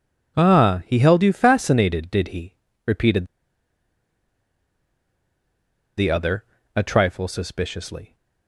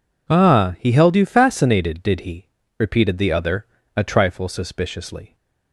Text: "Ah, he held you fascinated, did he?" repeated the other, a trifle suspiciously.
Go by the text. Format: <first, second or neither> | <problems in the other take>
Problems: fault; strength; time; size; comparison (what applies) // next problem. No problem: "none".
second | pauses between "repeated" and "the"; strong; at 3.2 s; 2.7 s long